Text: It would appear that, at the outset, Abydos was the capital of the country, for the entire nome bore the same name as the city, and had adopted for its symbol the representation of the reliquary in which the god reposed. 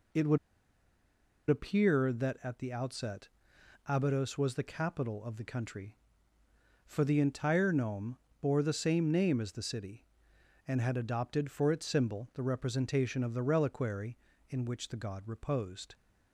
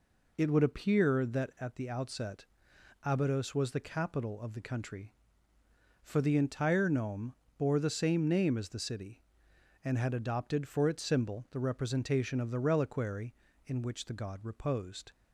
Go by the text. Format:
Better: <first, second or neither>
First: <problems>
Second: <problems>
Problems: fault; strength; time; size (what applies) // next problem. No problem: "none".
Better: second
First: pauses between "would" and "appear"; at 0.3 s; 1.1 s long // pauses between "nome" and "bore"; slight; at 8.1 s; 0.24 s long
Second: pauses between "nome" and "bore"; slight; at 7.3 s; 0.24 s long